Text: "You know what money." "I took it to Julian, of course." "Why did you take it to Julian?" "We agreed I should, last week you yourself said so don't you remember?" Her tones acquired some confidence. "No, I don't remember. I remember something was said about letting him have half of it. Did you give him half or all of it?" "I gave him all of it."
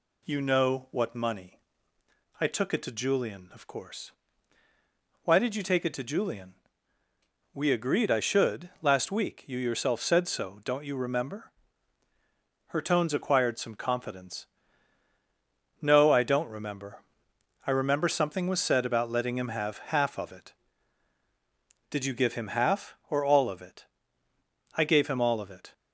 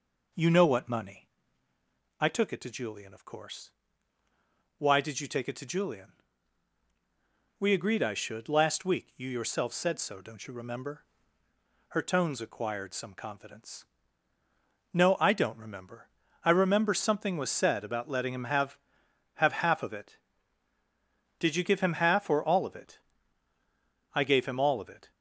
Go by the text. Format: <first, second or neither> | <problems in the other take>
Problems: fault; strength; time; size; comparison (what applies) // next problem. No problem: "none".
first | says "have" twice; at 19.3 s